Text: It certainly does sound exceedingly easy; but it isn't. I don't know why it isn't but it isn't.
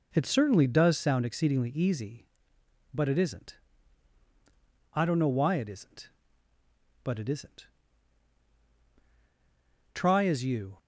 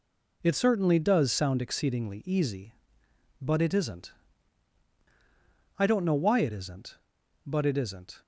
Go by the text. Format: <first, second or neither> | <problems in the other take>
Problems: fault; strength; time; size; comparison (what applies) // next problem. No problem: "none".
second | goes on to say "Try as you"; noticeable; from 9.9 s on; 0.82 s long